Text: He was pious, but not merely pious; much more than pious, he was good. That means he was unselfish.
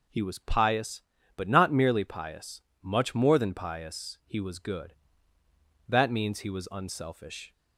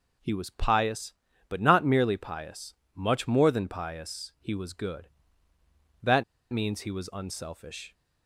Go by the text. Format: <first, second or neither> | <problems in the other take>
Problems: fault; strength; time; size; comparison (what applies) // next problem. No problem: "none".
first | pauses between "That" and "means"; slight; at 6.2 s; 0.29 s long